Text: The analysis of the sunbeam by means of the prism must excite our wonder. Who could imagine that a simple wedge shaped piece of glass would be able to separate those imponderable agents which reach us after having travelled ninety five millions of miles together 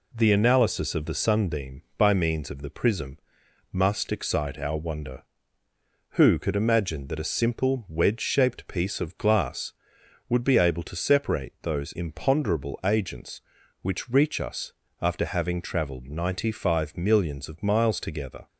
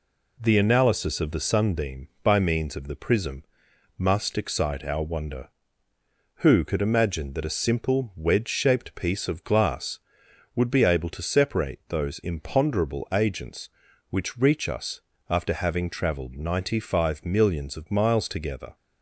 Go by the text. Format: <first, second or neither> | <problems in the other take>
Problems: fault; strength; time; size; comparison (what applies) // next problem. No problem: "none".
neither | pauses between "prism" and "must"; noticeable; the same in both // pauses between "us" and "after"; slight; the same in both